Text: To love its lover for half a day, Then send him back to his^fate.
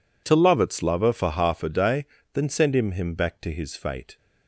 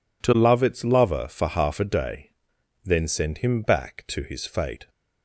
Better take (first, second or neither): second